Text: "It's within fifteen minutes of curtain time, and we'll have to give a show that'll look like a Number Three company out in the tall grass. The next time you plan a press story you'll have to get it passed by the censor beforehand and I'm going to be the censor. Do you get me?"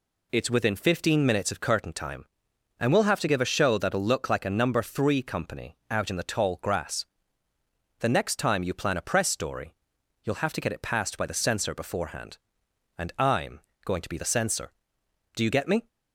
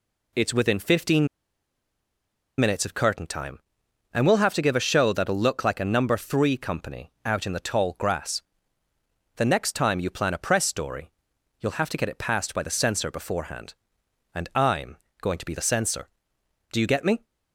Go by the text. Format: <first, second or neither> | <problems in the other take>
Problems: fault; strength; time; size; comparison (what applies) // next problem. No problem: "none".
first | pauses between "fifteen" and "minutes"; strong; at 1.2 s; 1.3 s long // pauses between "story" and "you'll"; noticeable; at 11.0 s; 0.50 s long; noticeable in the first // pauses between "I'm" and "going"; slight; at 14.9 s; 0.24 s long; slight in the first